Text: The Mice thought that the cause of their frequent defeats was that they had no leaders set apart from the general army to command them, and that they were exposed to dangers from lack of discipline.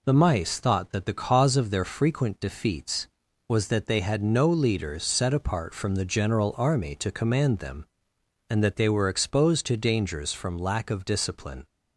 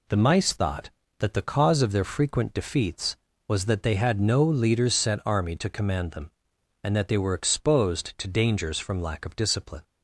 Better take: first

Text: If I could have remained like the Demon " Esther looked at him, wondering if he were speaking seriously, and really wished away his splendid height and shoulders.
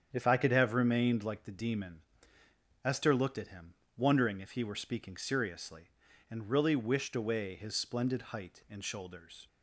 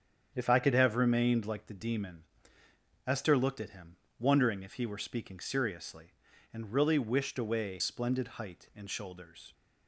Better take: first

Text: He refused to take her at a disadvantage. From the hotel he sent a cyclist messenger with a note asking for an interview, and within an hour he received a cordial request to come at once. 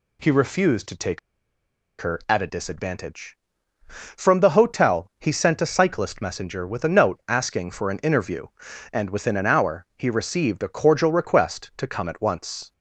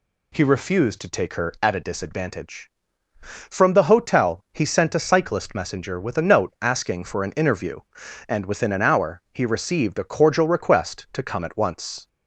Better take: second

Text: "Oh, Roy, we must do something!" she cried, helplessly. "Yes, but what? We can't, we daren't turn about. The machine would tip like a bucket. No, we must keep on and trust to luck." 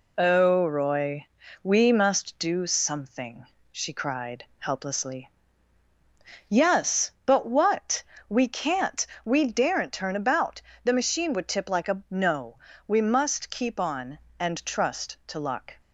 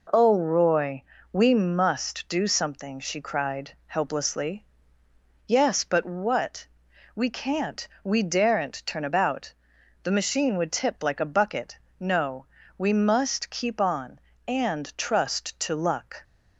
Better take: second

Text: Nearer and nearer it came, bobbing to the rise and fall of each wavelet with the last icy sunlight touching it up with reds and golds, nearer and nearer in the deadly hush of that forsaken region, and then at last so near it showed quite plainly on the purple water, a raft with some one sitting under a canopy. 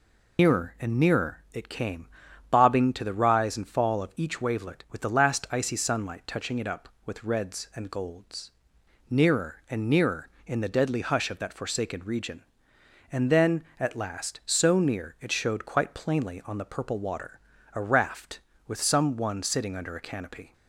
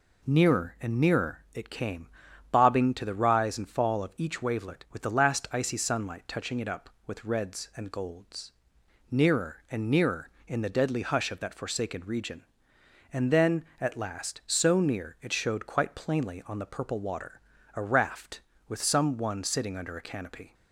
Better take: second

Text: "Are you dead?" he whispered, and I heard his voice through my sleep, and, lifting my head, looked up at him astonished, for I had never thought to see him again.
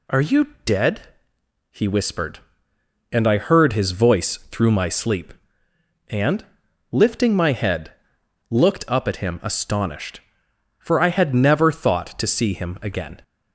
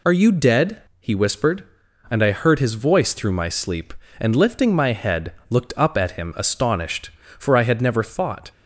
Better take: first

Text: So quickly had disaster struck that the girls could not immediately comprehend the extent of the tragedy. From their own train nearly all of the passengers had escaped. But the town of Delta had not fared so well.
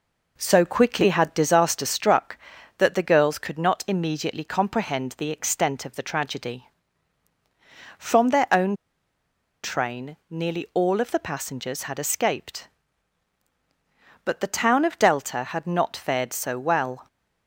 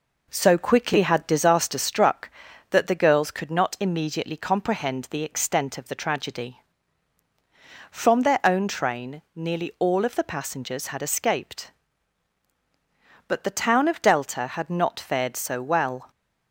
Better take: second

